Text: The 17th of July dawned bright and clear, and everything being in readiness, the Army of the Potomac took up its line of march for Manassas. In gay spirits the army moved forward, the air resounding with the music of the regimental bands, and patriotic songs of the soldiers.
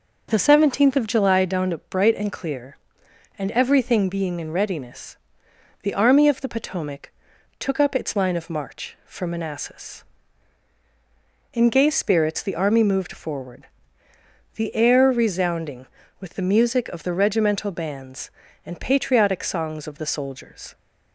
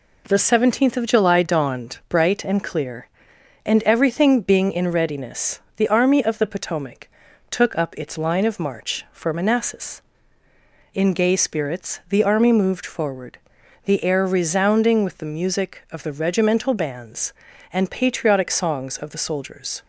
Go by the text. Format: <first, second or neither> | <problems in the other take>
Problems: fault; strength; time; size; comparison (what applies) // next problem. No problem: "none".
neither | pauses between "Potomac" and "took"; the same in both